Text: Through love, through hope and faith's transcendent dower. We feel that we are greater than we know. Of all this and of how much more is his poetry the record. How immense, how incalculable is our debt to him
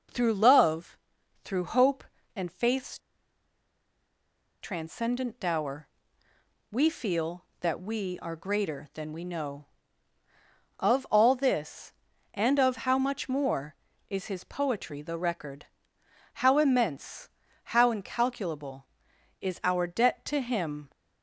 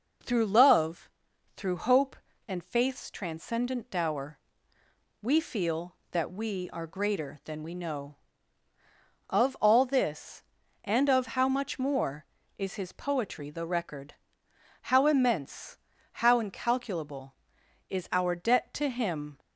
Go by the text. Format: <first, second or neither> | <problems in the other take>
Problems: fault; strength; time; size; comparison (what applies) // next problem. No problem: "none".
second | pauses between "faith's" and "transcendent"; strong; at 2.9 s; 1.6 s long